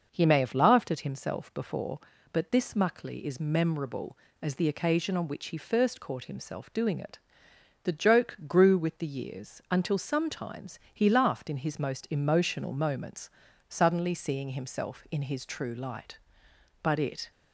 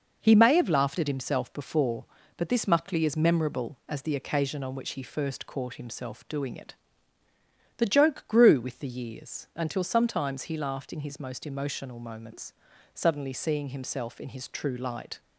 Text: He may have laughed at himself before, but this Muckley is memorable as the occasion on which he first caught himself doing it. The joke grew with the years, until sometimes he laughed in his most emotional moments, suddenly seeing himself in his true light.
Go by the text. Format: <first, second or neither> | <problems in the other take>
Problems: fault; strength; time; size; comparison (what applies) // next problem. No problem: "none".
second | goes on to say "But it"; slight; from 16.8 s on; 0.48 s long